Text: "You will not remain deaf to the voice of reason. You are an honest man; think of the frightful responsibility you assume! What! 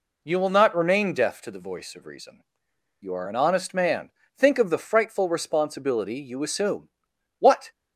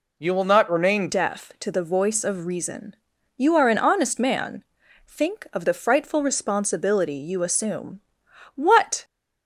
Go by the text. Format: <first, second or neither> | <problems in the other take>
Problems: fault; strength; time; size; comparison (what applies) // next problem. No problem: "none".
first | changes voice at "deaf"; from 1.0 s on; 8.0 s long